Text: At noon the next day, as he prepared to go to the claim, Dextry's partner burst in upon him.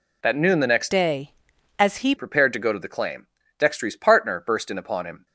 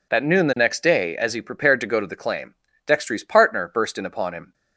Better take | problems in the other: second | changes voice from "day" to "he"; from 0.9 to 2.1 s; 1.2 s long

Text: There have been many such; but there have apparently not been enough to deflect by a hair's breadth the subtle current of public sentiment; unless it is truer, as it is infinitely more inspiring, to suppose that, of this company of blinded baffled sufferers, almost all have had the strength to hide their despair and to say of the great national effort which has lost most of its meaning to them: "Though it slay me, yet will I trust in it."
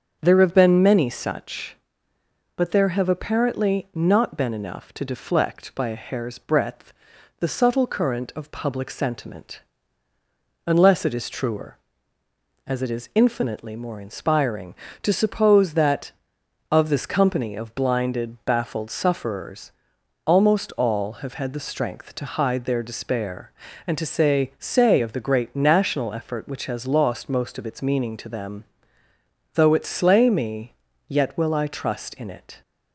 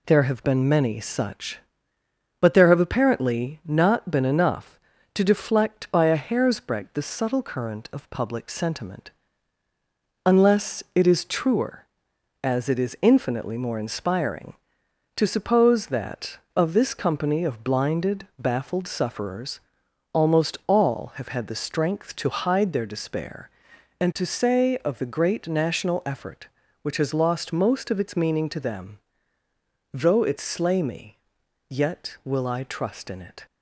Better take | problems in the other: second | starts louder than the rest; until 1.2 s; 7 dB // pauses between "breadth" and "the"; noticeable; at 6.9 s; 0.46 s long // says "say" twice; at 24.5 s

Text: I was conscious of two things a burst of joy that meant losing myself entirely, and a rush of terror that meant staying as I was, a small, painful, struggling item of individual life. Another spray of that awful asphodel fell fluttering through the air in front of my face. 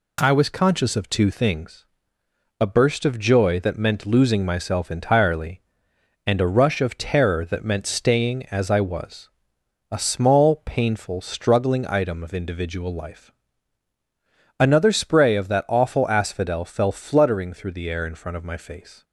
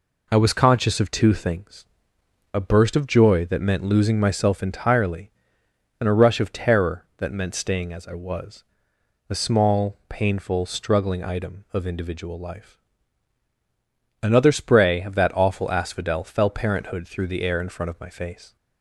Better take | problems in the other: first | pauses between "things" and "a"; noticeable; at 1.8 s; 0.68 s long; noticeable in the first // says "parenthood" for "fluttering"; at 16.4 s

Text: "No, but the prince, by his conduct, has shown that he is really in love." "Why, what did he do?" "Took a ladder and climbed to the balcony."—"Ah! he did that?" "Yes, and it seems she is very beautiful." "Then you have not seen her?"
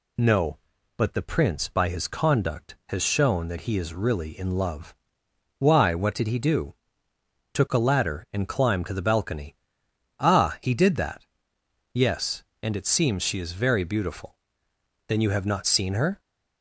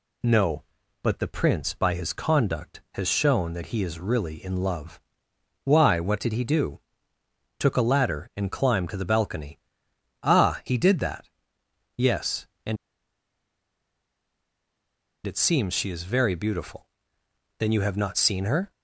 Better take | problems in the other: first | pauses between "and" and "it"; strong; at 12.7 s; 2.5 s long

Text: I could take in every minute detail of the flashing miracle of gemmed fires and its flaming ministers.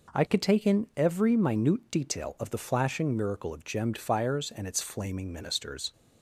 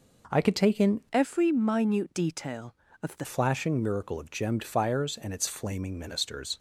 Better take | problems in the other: first | changes voice from "every" to "the"; from 1.1 to 3.2 s; 2.1 s long

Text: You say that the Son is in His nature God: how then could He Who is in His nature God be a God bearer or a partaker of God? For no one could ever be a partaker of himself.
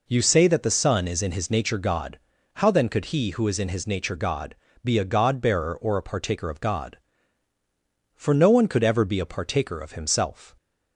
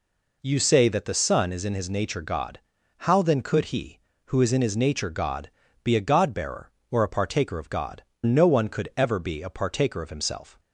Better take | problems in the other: first | pauses between "God" and "be"; slight; at 5.4 s; 0.34 s long; slight in the first // skips "For"; at 8.1 s

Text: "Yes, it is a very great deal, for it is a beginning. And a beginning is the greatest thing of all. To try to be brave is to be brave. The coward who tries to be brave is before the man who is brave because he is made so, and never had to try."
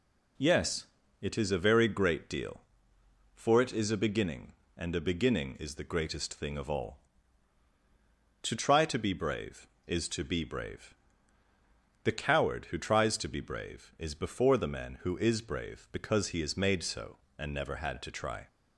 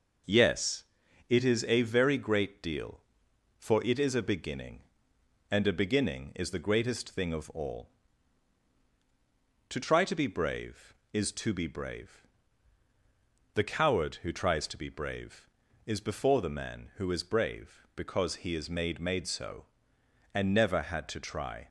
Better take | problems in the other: first | says "made" twice; at 18.9 s

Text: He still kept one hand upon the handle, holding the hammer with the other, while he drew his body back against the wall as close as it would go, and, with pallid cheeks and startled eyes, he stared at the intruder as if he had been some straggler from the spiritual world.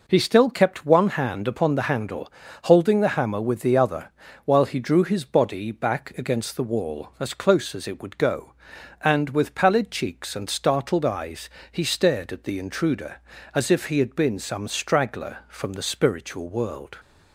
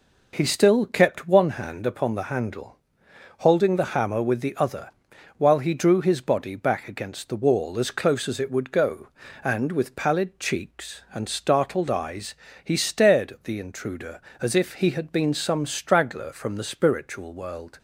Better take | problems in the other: neither | none

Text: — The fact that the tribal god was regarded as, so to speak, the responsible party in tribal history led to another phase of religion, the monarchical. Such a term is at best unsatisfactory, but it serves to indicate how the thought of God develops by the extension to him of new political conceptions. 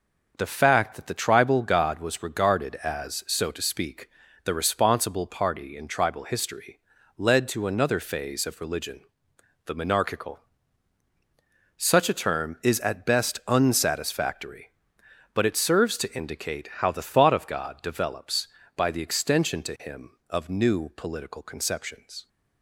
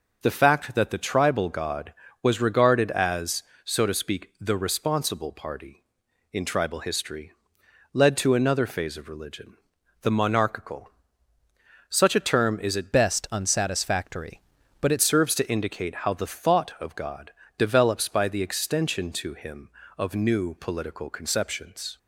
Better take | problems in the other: first | pauses between "history" and "led"; noticeable; at 7.3 s; 0.60 s long; also in the first // changes voice from "best" to "it"; from 12.9 to 15.0 s; 2.1 s long // pauses between "God" and "develops"; slight; at 17.3 s; 0.26 s long

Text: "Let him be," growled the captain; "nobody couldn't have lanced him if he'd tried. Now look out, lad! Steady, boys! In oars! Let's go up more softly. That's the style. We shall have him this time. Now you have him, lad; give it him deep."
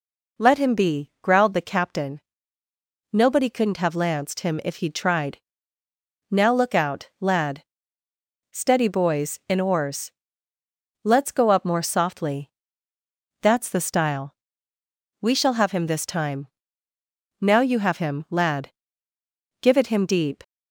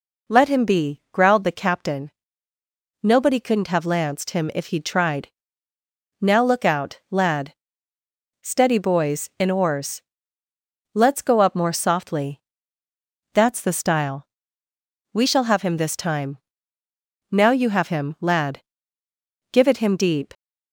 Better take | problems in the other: neither | none

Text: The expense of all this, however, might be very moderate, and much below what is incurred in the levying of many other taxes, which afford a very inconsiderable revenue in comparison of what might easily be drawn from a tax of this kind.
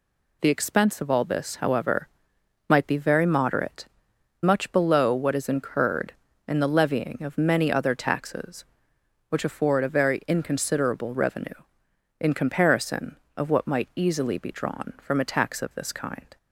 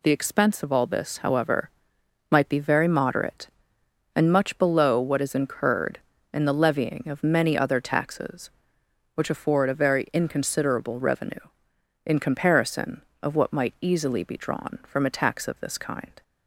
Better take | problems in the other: second | skips "and"; at 4.1 s

